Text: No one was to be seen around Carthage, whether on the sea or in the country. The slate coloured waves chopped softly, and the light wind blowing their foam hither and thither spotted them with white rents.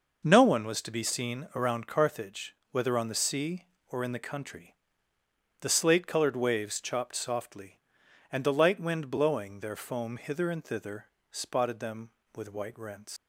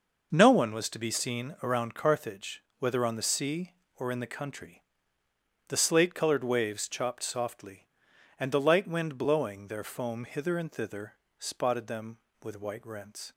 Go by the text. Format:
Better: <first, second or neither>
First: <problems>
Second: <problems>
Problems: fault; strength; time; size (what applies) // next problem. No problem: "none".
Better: second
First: pauses between "thither" and "spotted"; slight; at 11.0 s; 0.26 s long // leaves "rents" unfinished; at 13.1 s; 80 ms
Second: pauses between "thither" and "spotted"; slight; at 11.1 s; 0.26 s long